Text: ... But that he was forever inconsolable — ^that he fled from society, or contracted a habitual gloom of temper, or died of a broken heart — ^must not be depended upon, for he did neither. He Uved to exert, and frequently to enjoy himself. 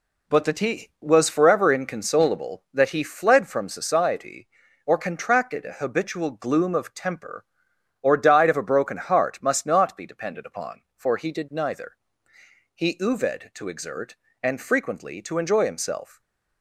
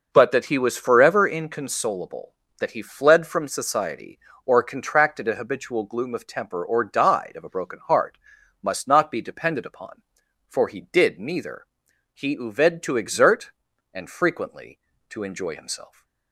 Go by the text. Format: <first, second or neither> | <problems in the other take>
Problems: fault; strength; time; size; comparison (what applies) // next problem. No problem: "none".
neither | none